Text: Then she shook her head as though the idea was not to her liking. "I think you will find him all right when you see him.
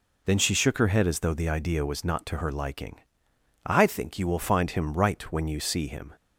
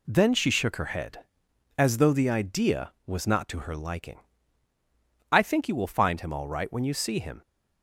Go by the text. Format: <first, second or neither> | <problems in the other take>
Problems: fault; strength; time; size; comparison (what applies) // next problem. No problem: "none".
second | skips "all"; at 4.9 s